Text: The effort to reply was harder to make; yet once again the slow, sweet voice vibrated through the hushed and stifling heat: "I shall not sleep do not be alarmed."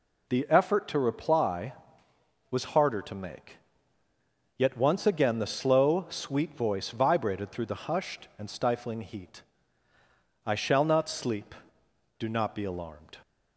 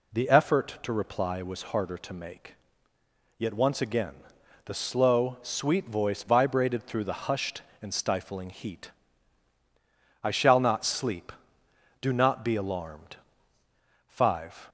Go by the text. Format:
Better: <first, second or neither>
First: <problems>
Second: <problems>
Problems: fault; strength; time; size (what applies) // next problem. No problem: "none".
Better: first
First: none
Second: pauses between "again" and "the"; noticeable; at 4.1 s; 0.50 s long // goes on to say "Five"; from 14.0 s on; 0.60 s long